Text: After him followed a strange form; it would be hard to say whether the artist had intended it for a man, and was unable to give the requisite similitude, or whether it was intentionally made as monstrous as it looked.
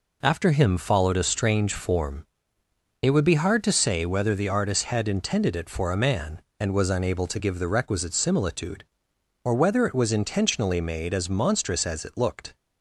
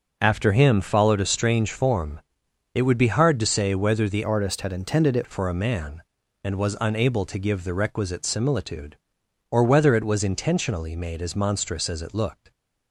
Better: first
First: none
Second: starts louder than the rest; until 1.2 s; 6.5 dB // changes voice from "artist" to "it"; from 4.2 to 5.2 s; 1.0 s long

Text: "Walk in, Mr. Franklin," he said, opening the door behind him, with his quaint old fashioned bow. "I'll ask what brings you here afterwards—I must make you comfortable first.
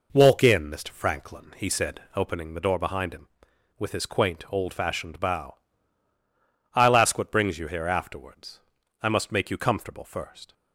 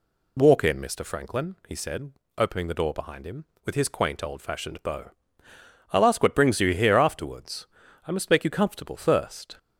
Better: neither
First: none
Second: none

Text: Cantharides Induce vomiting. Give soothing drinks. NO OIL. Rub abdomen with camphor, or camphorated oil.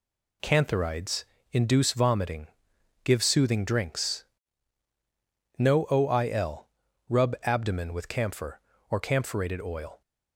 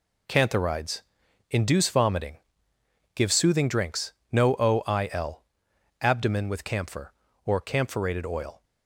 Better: first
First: pauses between "Cantharides" and "Induce"; slight; at 1.2 s; 0.26 s long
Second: pauses between "Cantharides" and "Induce"; noticeable; at 1.0 s; 0.50 s long // skips "Rub"; at 5.7 s

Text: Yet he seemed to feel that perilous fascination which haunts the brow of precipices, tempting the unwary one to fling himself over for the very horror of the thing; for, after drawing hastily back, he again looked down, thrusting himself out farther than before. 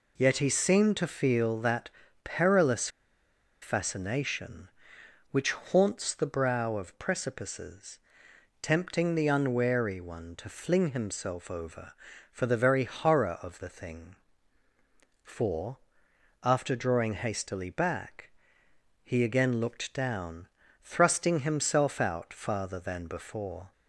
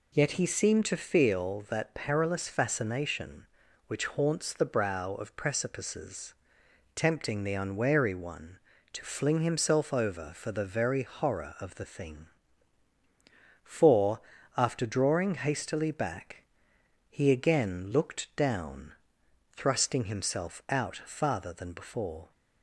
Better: second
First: pauses between "that" and "perilous"; slight; at 1.9 s; 0.34 s long // pauses between "perilous" and "fascination"; noticeable; at 2.8 s; 0.73 s long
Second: none

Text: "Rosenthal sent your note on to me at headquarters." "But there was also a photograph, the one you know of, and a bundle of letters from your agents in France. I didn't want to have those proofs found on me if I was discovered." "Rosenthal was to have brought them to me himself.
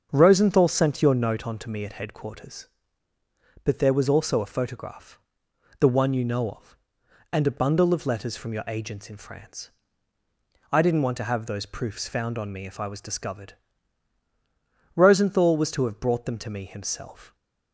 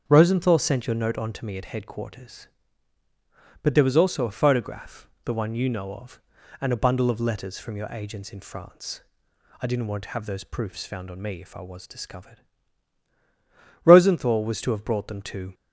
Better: first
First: starts louder than the rest; until 1.1 s; 7 dB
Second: starts louder than the rest; strong; until 1.0 s; 7.5 dB // stops before "me himself"; at 15.5 s

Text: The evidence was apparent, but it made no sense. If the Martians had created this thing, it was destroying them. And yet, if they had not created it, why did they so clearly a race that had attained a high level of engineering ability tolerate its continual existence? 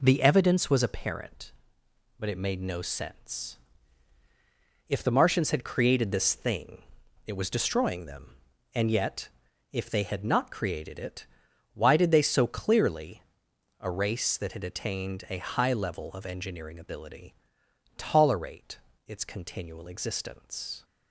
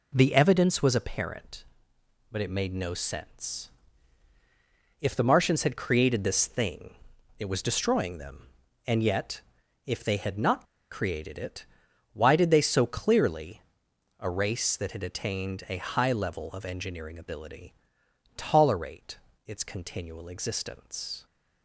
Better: first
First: pauses between "clearly" and "a"; noticeable; at 13.2 s; 0.58 s long // pauses between "ability" and "tolerate"; noticeable; at 17.3 s; 0.64 s long // pauses between "tolerate" and "its"; slight; at 18.7 s; 0.28 s long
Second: pauses between "not" and "created"; slight; at 10.6 s; 0.25 s long // pauses between "clearly" and "a"; noticeable; at 13.6 s; 0.58 s long // pauses between "ability" and "tolerate"; noticeable; at 17.7 s; 0.64 s long // pauses between "tolerate" and "its"; slight; at 19.1 s; 0.28 s long

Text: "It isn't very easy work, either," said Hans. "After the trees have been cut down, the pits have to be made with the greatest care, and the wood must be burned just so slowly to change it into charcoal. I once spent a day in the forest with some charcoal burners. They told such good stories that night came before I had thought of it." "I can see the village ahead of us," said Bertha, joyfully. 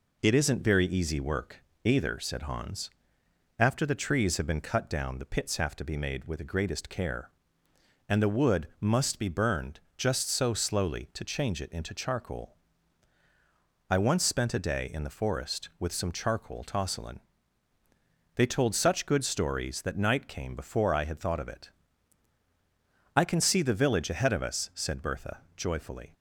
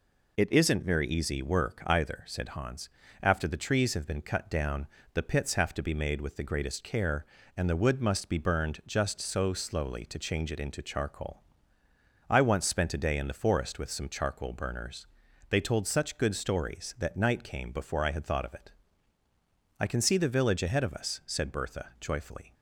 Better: second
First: pauses between "burned" and "just"; slight; at 9.7 s; 0.16 s long // says "tosselin" for "burners"; at 16.6 s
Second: none

